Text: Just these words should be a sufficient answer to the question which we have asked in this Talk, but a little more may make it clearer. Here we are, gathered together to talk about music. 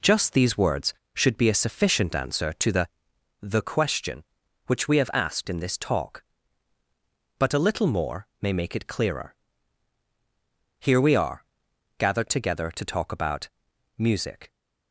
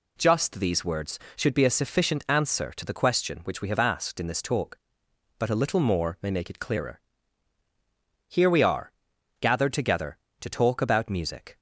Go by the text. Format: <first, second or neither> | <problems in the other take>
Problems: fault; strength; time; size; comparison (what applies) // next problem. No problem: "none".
second | says "the" twice; at 3.4 s // pauses between "more" and "may"; slight; at 8.2 s; 0.16 s long // pauses between "about" and "music"; noticeable; at 13.4 s; 0.50 s long